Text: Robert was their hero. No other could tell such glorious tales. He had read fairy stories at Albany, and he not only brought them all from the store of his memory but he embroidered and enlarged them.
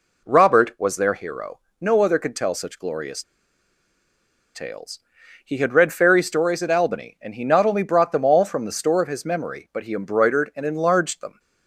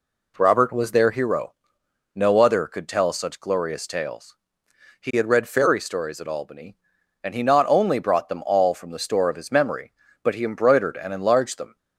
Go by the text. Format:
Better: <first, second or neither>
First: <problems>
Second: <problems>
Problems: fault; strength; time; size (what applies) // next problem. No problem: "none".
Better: second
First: pauses between "glorious" and "tales"; strong; at 3.2 s; 1.3 s long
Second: none